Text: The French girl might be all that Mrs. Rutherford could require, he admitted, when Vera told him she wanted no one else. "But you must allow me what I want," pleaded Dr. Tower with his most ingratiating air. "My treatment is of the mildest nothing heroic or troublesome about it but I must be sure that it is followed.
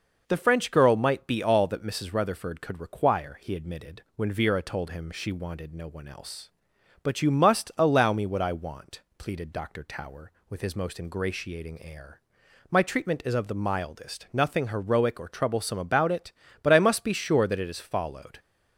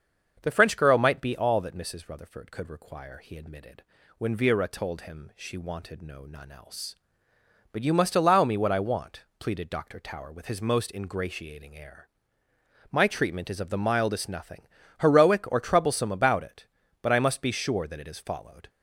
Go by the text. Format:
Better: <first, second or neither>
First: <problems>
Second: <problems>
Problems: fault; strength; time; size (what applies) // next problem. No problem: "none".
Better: first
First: none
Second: starts louder than the rest; until 1.4 s; 6.5 dB // says "none" for "one"; at 6.2 s // pauses between "nothing" and "heroic"; slight; at 14.6 s; 0.32 s long